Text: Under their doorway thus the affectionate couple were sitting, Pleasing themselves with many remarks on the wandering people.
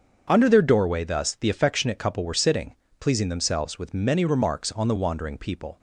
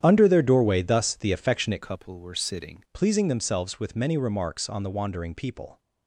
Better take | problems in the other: first | starts louder than the rest; strong; until 1.0 s; 9.5 dB; also in the first // changes voice from "couple" to "sitting"; from 1.8 to 2.8 s; 1.0 s long

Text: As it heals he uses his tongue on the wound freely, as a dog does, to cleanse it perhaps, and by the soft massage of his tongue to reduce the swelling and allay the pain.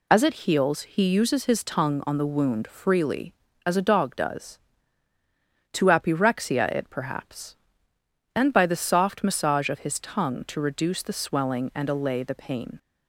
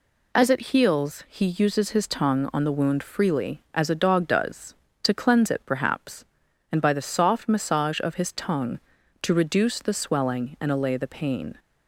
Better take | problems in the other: second | says "apyrexia" for "cleanse"; at 5.8 s

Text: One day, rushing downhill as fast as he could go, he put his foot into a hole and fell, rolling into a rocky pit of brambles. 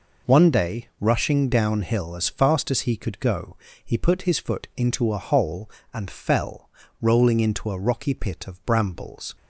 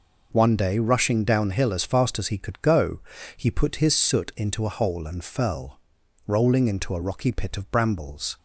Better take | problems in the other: first | says "soot" for "foot"; at 3.9 s

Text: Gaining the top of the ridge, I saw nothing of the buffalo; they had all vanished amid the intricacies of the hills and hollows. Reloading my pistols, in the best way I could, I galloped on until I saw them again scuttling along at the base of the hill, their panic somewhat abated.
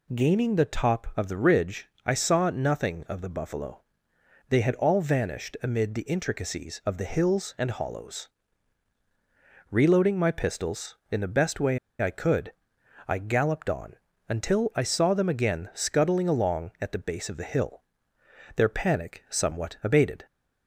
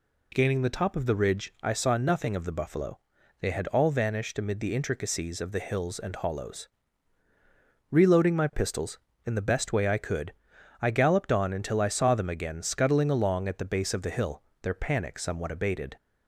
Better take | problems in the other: second | pauses between "way" and "I"; slight; at 11.7 s; 0.23 s long // pauses between "on" and "until"; slight; at 13.9 s; 0.32 s long

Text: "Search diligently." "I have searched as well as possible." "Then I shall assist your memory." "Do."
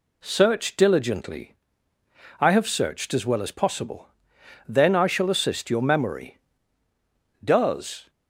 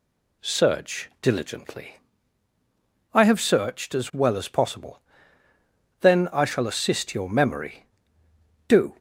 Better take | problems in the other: second | says "Does" for "Do"; at 7.4 s

